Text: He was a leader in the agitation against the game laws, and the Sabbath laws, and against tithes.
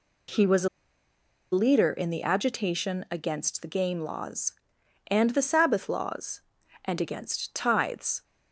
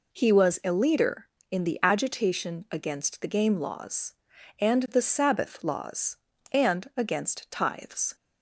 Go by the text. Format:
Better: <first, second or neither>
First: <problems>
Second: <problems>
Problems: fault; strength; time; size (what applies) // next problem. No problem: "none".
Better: second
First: pauses between "a" and "leader"; noticeable; at 0.6 s; 0.84 s long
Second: none